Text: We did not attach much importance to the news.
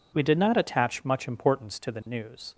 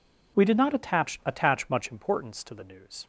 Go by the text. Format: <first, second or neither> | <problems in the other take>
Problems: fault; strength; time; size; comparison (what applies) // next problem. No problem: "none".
first | says "attach" twice; at 1.2 s